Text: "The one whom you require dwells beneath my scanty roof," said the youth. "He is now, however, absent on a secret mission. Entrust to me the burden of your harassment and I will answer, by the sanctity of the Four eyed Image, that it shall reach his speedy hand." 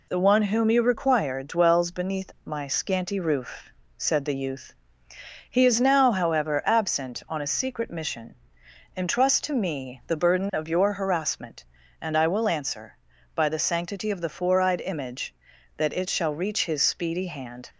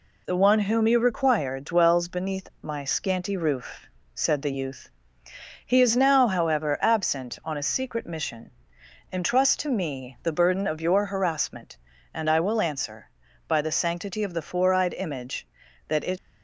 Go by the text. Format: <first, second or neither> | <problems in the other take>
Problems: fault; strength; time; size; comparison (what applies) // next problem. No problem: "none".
first | stops before "shall reach his speedy hand"; at 16.1 s